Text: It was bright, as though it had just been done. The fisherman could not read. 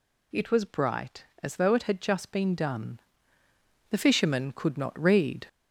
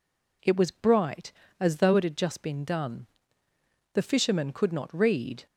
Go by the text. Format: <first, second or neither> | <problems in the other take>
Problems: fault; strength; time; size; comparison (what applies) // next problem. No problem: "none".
second | gets louder; throughout; 3.5 dB